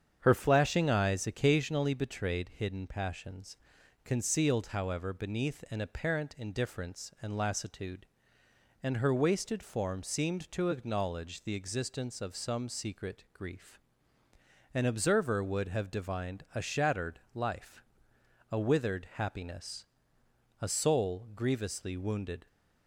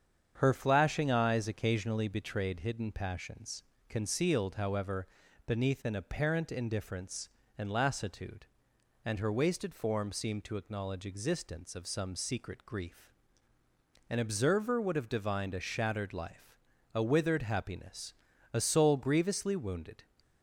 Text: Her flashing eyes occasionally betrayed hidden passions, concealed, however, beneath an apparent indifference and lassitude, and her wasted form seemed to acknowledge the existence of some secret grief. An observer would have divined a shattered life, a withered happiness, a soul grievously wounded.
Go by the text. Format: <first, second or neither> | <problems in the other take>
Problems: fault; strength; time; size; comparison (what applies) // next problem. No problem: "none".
first | starts louder than the rest; strong; until 1.3 s; 8 dB; strong in the first // skips "the"; at 11.0 s